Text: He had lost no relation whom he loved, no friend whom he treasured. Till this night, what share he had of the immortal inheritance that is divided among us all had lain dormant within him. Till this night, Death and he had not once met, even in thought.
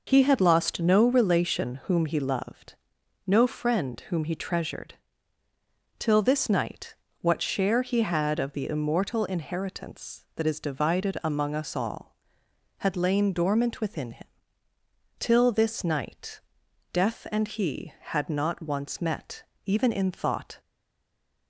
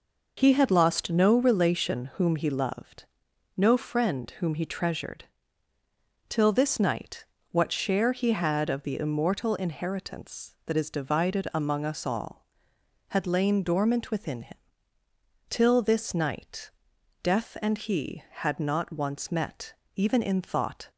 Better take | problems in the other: second | stays silent after the last word; slight; from 20.6 s on; 0.8 s long

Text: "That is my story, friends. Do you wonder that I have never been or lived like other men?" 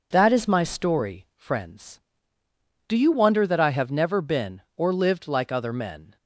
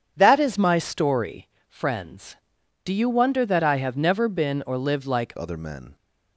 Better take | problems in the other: first | changes voice at "other"; from 5.3 s on; 0.6 s long

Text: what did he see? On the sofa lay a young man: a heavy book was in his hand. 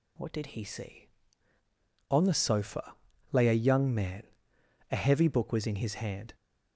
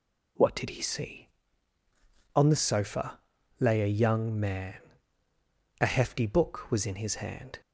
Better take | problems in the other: first | pauses between "sofa" and "lay"; at 3.1 s; 0.40 s long; also in the first // says "hefty" for "heavy"; at 5.8 s

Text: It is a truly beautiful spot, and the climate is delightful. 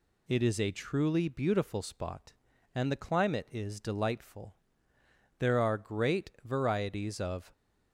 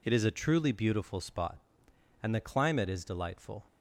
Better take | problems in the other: second | goes on to say "There are great varieties of"; strong; from 5.3 s on; 2.1 s long

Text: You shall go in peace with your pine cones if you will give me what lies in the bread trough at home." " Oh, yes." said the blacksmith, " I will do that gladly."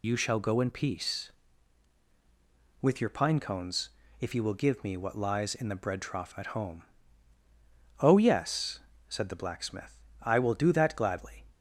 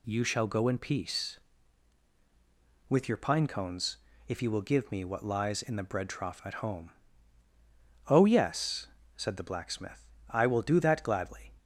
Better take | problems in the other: second | loses the start of "You"; at 0.0 s; 75 ms // pauses between "cones" and "if"; slight; at 3.8 s; 0.30 s long; slight in the second

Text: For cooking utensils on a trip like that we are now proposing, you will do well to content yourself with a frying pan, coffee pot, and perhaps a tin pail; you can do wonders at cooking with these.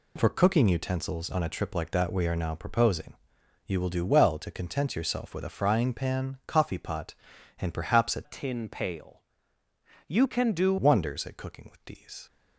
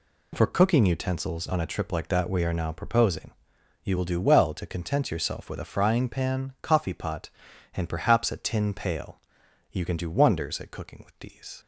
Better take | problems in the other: second | changes voice from "tin" to "do"; from 8.2 to 10.7 s; 2.5 s long

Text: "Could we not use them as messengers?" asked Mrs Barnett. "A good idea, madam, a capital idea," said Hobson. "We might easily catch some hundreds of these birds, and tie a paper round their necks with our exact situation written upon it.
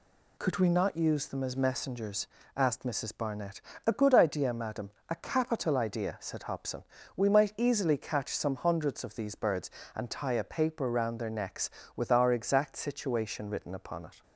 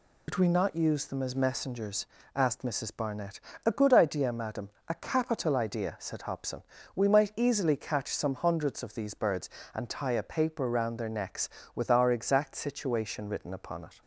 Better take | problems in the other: first | loses the start of "Could"; at 0.2 s; 110 ms

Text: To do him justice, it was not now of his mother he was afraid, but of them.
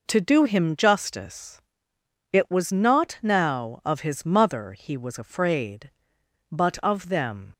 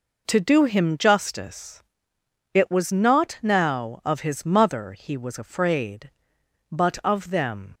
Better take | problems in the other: neither | none

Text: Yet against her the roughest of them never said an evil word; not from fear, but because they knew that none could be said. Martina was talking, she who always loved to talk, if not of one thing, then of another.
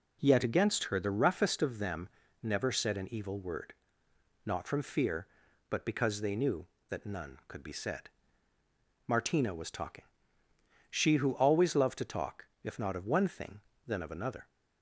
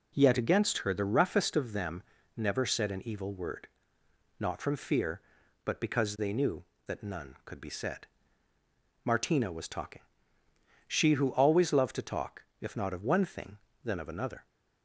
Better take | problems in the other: neither | pauses between "them" and "never"; slight; the same in both

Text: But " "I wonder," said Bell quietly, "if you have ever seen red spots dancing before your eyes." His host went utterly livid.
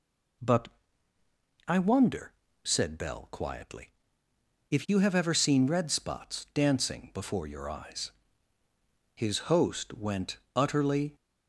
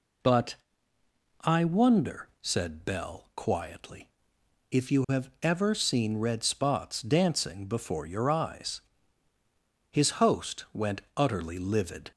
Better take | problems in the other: second | pauses between "went" and "utterly"; slight; at 10.3 s; 0.16 s long // stops before "livid"; at 11.1 s

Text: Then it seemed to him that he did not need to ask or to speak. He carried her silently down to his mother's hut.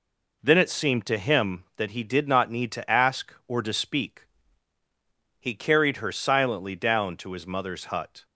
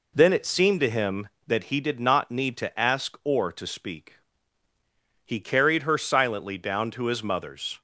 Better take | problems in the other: first | stops before "hut"; at 7.7 s

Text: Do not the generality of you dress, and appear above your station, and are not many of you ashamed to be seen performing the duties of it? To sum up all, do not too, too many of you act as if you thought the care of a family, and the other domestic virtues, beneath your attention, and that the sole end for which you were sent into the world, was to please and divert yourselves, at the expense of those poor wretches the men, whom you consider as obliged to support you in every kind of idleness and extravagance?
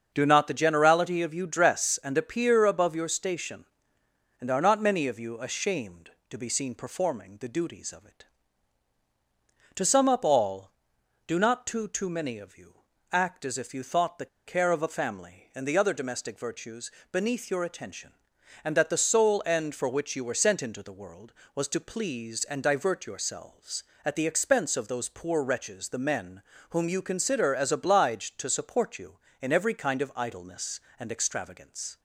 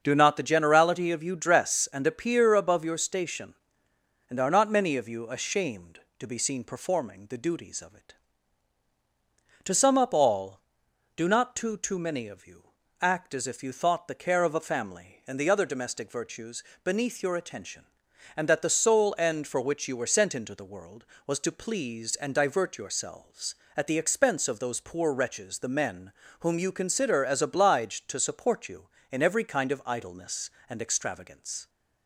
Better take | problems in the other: second | starts louder than the rest; until 1.1 s; 7 dB; also in the second // pauses between "you" and "act"; slight; at 12.7 s; 0.36 s long; slight in the second // pauses between "the" and "care"; slight; at 14.2 s; 0.19 s long

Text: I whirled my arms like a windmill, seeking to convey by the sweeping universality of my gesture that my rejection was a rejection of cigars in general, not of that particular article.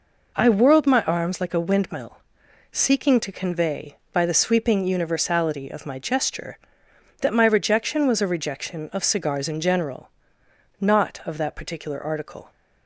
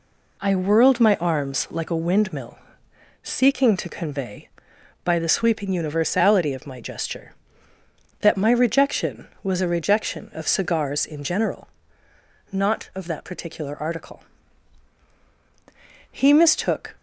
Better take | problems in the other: first | goes on to say "He mistook"; noticeable; from 16.1 s on; 0.86 s long

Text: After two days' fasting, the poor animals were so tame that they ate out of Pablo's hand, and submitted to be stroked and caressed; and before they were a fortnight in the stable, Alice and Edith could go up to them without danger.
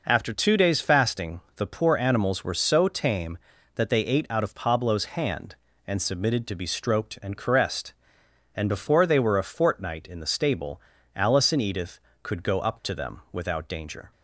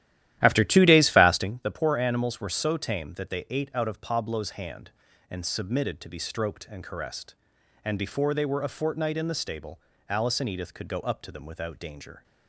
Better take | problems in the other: first | starts louder than the rest; strong; until 1.5 s; 13 dB

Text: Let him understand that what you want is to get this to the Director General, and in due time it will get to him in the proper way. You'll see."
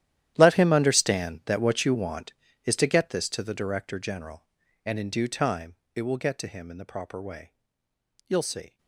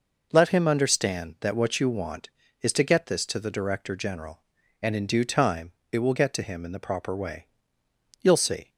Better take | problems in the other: second | gets quieter; strong; throughout; 18 dB // pauses between "time" and "it"; slight; at 5.7 s; 0.18 s long; slight in the second

